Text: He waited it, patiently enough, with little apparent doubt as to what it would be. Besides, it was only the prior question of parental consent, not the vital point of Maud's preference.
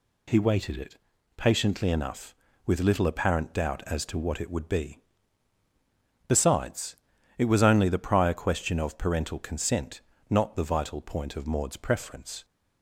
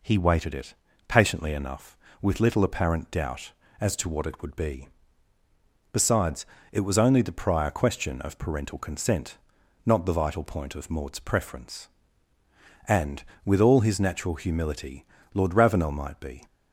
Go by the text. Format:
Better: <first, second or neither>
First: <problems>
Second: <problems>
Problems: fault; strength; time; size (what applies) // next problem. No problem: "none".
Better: first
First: none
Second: goes on to say "And with all his natural humility Lord Ravenel might be"; strong; from 12.8 s on; 3.5 s long